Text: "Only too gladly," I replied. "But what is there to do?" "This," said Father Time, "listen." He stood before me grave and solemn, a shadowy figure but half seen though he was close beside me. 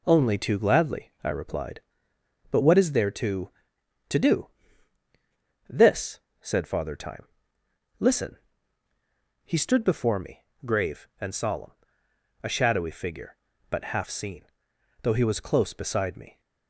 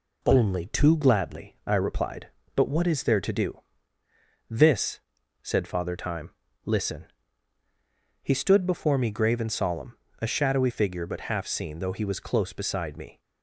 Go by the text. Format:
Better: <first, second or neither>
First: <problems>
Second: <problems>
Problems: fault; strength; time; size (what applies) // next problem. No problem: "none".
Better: second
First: says "to" twice; at 4.0 s // pauses between "me" and "grave"; slight; at 10.4 s; 0.22 s long // pauses between "seen" and "though"; noticeable; at 14.4 s; 0.60 s long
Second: none